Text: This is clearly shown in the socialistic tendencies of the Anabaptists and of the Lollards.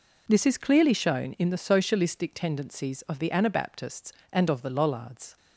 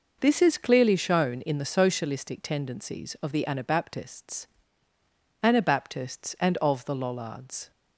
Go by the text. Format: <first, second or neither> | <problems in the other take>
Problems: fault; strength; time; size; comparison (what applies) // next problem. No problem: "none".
first | says "Anabaptists" twice; at 5.4 s